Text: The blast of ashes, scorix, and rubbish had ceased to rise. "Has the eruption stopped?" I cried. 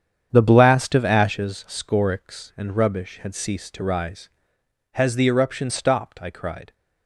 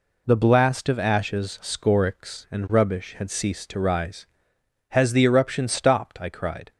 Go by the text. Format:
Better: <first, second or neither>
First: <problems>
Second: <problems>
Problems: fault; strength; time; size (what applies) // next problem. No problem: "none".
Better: second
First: starts louder than the rest; strong; until 1.5 s; 8.5 dB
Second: none